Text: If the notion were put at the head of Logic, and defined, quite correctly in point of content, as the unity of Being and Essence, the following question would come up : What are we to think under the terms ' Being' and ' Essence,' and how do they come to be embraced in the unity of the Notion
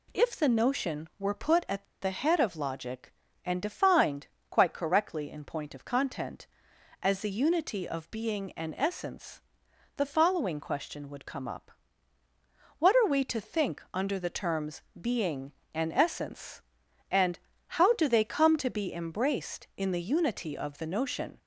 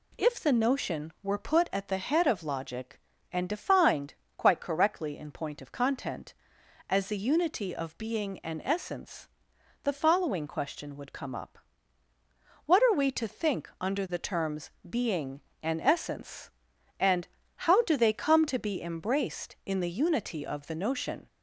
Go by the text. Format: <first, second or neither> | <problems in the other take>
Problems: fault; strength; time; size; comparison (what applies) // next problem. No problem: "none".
second | pauses between "at" and "the"; slight; at 1.8 s; 0.18 s long // pauses between "and" and "how"; slight; at 17.3 s; 0.30 s long; slight in the second